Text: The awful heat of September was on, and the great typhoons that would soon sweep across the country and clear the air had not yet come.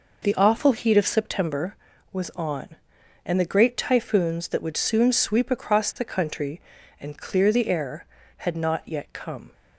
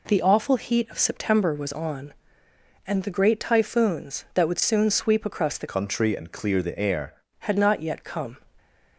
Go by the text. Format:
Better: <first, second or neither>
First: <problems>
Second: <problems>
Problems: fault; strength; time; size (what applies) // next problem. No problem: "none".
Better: first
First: none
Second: changes voice from "country" to "air"; from 5.6 to 7.2 s; 1.6 s long